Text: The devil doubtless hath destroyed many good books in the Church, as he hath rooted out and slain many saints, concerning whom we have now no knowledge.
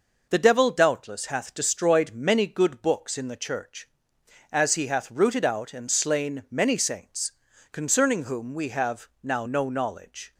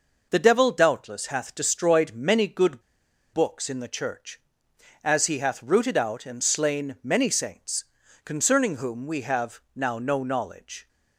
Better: first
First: none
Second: pauses between "good" and "books"; noticeable; at 2.8 s; 0.51 s long

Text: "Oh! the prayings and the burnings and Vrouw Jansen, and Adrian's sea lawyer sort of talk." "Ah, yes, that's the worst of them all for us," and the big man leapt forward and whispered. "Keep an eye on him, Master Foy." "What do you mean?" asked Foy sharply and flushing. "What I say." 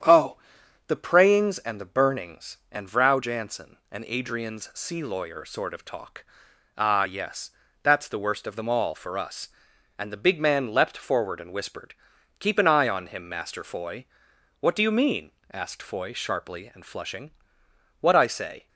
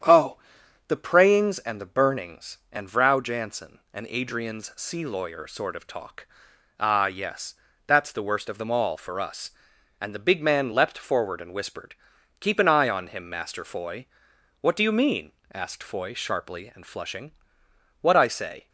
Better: neither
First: starts louder than the rest; strong; until 1.5 s; 9 dB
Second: starts louder than the rest; strong; until 1.5 s; 9 dB

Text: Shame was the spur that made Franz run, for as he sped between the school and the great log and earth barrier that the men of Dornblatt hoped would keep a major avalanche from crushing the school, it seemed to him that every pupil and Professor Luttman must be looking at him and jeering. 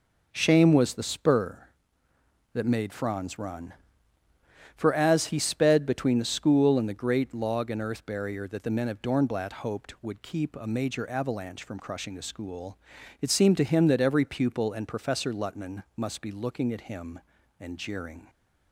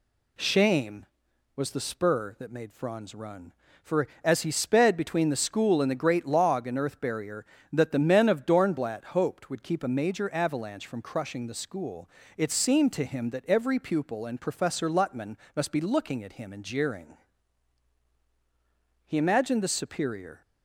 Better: first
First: none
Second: pauses between "Luttman" and "must"; slight; at 15.3 s; 0.20 s long // goes on to say "He imagined the superior"; from 19.0 s on; 1.3 s long

